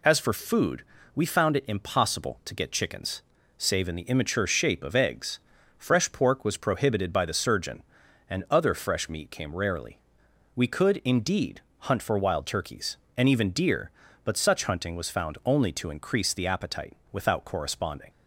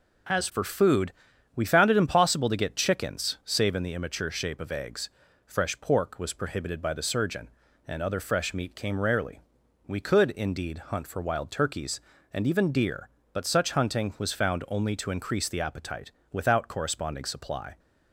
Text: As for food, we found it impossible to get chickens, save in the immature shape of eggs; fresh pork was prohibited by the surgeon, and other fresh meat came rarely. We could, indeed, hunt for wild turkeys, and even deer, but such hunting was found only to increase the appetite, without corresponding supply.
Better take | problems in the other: second | stops before "supply"; at 18.0 s

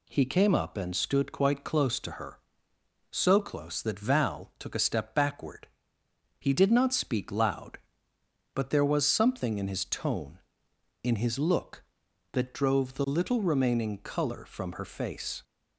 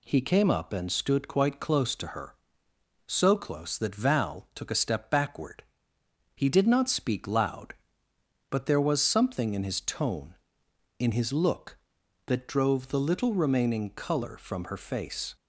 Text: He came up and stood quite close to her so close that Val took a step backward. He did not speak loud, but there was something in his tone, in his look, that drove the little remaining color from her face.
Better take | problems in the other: neither | none

